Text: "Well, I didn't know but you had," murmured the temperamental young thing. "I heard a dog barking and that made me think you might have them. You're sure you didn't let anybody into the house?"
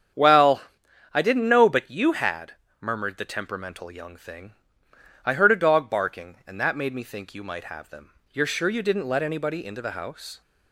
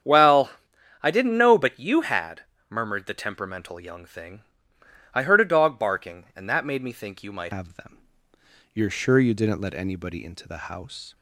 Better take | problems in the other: first | starts louder than the rest; strong; until 1.5 s; 8.5 dB; strong in the first // changes voice at "have"; from 7.5 s on; 3.6 s long

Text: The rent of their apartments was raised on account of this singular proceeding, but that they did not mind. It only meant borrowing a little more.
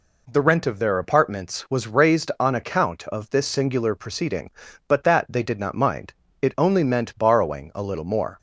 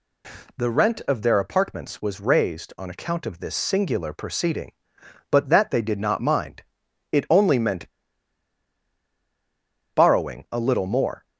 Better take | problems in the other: first | pauses between "meant" and "borrowing"; strong; at 7.8 s; 2.0 s long

